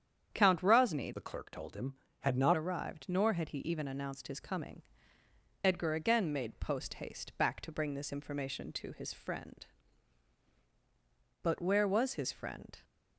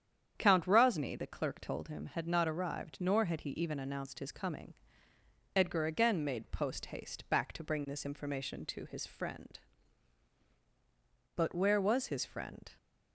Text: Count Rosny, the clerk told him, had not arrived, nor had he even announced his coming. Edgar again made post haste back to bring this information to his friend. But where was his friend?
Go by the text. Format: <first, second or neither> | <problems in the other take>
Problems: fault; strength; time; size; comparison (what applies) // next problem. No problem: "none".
second | starts louder than the rest; strong; until 1.3 s; 8.5 dB; strong in the second // changes voice from "the" to "not"; from 1.1 to 2.5 s; 1.4 s long